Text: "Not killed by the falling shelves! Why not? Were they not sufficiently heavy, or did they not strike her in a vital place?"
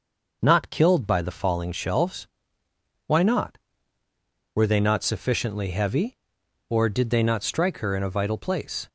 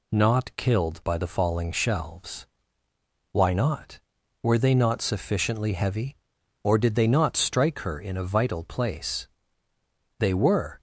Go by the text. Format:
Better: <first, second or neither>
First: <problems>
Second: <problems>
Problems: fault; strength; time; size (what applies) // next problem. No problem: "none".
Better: first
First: none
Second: goes on to say "They were"; noticeable; from 10.1 s on; 0.62 s long